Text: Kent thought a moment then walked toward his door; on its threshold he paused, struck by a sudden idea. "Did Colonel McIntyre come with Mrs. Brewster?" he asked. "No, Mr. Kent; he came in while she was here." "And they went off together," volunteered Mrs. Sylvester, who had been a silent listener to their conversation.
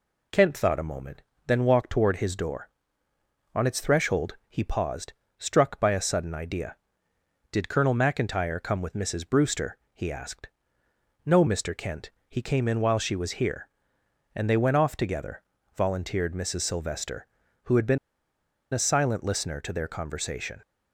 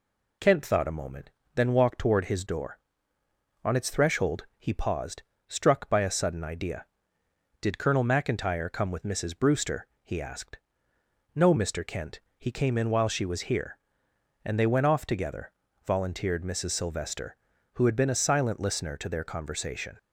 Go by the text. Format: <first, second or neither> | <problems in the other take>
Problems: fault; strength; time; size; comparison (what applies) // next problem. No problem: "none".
second | pauses between "moment" and "then"; slight; at 1.2 s; 0.24 s long; slight in the second // pauses between "been" and "a"; noticeable; at 17.9 s; 0.75 s long